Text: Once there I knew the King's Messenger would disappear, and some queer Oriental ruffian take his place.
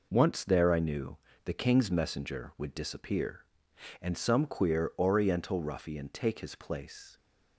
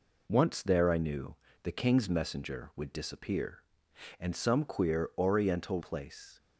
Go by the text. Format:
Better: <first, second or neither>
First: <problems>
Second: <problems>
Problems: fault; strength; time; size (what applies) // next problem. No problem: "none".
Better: first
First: pauses between "knew" and "the"; slight; at 1.1 s; 0.28 s long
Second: pauses between "knew" and "the"; slight; at 1.3 s; 0.28 s long // skips "ruffian take his"; at 5.8 s